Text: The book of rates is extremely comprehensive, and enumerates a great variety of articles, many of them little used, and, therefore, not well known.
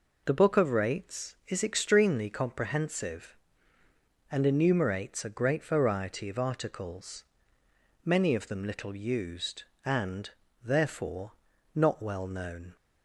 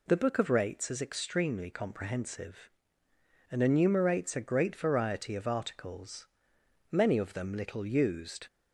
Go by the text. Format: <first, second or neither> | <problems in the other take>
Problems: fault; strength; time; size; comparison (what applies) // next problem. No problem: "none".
first | stops before "and therefore not well known"; at 8.4 s